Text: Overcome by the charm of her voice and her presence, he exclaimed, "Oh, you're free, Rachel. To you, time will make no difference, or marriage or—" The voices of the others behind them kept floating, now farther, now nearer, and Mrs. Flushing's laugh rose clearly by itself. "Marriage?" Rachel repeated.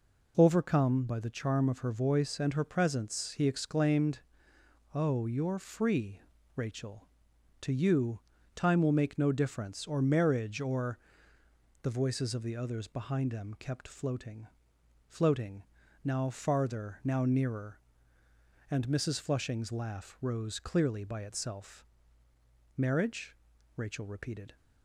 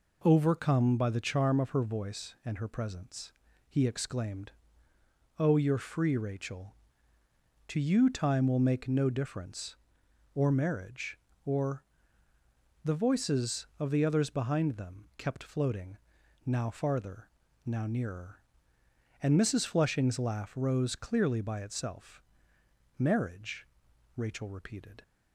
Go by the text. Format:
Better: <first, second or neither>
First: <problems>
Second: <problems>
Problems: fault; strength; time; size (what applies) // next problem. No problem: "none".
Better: second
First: says "floating" twice; at 15.0 s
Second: none